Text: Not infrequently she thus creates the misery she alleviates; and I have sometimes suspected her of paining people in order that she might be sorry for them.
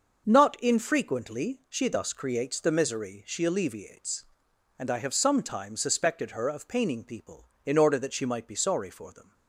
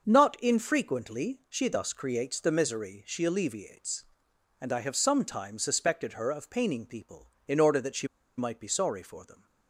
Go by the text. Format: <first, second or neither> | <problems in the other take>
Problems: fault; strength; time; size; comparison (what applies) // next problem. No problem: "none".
first | starts louder than the rest; until 1.0 s; 6 dB; also in the first // pauses between "she" and "might"; slight; at 8.0 s; 0.30 s long